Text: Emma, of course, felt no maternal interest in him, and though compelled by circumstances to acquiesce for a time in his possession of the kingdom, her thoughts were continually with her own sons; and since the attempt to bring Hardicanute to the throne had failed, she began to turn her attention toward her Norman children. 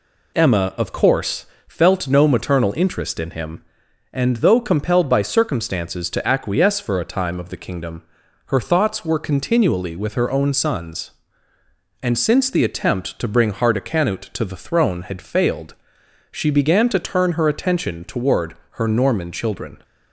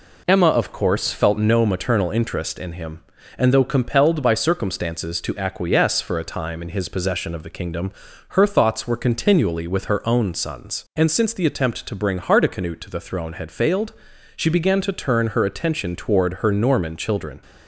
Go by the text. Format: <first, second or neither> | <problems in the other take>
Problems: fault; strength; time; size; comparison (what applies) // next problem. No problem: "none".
second | skips "in his possession"; at 7.3 s